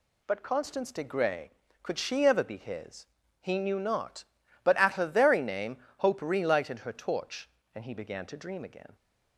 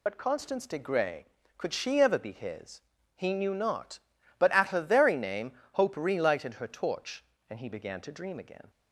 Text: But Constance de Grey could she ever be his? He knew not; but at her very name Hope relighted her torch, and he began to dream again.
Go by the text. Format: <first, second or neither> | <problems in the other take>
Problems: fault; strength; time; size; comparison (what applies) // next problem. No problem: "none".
first | loses the start of "But"; at 0.0 s; 60 ms